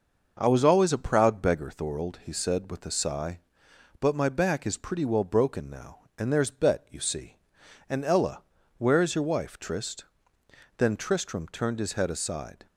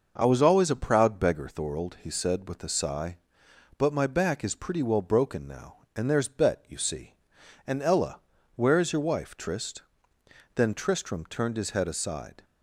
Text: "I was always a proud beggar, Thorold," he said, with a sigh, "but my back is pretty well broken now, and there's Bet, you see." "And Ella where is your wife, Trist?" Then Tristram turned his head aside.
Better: neither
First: pauses between "Ella" and "where"; slight; at 8.4 s; 0.34 s long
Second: pauses between "Ella" and "where"; slight; at 8.2 s; 0.34 s long

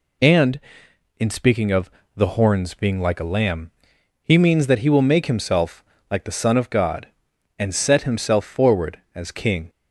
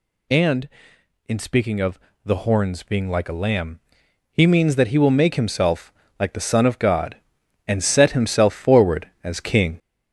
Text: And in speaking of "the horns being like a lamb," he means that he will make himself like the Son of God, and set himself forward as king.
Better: first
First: pauses between "of" and "the"; slight; at 1.9 s; 0.24 s long // pauses between "himself" and "like"; slight; at 5.8 s; 0.26 s long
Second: gets louder; noticeable; throughout; 5 dB // pauses between "of" and "the"; slight; at 2.0 s; 0.24 s long // pauses between "himself" and "like"; slight; at 5.9 s; 0.26 s long

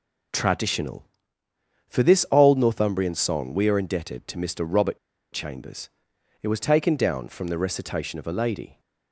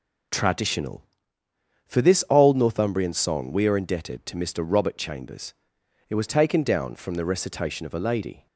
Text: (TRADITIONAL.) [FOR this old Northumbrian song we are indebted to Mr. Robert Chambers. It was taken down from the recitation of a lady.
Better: second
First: pauses between "Robert" and "Chambers"; slight; at 4.9 s; 0.35 s long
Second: none

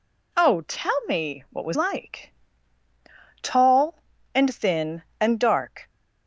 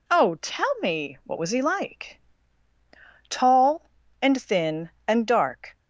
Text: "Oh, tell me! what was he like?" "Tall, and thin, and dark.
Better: second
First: skips "he"; at 1.7 s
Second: none

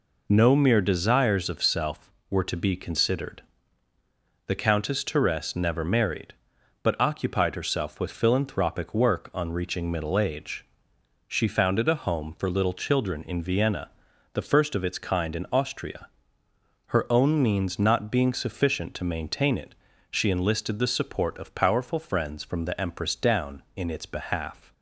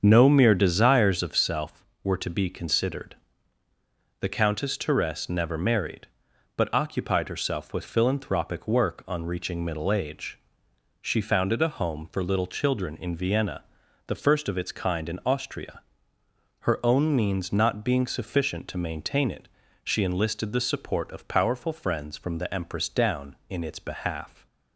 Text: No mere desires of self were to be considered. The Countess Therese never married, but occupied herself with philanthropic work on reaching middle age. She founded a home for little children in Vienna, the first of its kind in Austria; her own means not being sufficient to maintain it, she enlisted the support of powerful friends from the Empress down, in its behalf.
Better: first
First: none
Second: starts louder than the rest; until 1.5 s; 7 dB

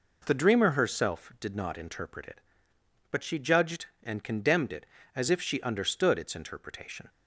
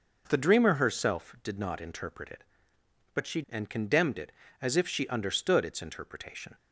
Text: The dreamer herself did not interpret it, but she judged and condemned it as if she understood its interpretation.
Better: first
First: none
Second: skips "judged"; at 3.4 s

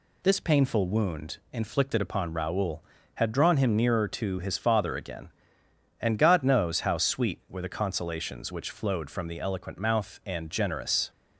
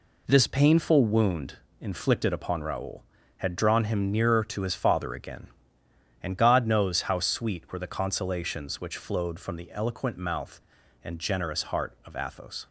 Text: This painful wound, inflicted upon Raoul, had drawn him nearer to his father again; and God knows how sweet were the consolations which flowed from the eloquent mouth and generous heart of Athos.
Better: second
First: stops before "heart of Athos"; at 11.0 s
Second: none

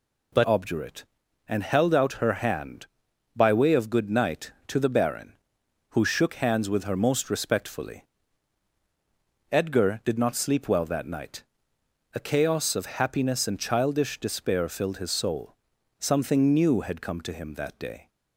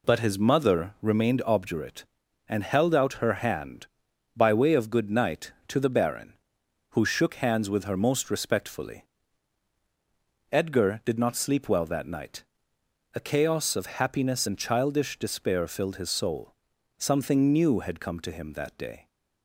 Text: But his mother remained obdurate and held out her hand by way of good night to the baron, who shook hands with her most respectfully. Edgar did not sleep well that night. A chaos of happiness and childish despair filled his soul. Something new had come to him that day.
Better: second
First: skips "his mother remained"; at 0.4 s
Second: none

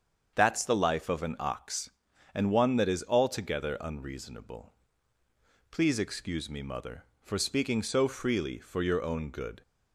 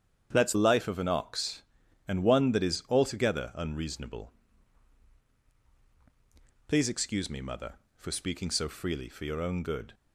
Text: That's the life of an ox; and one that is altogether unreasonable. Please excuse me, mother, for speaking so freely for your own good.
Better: first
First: starts louder than the rest; until 1.3 s; 7 dB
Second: starts louder than the rest; strong; until 1.3 s; 8 dB // skips "the"; at 0.5 s

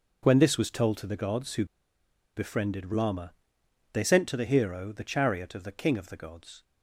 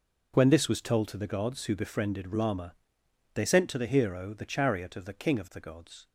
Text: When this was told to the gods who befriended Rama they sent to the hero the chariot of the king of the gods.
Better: second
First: pauses between "who" and "befriended"; noticeable; at 1.6 s; 0.70 s long // pauses between "Rama" and "they"; noticeable; at 3.3 s; 0.60 s long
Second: pauses between "Rama" and "they"; noticeable; at 2.7 s; 0.60 s long

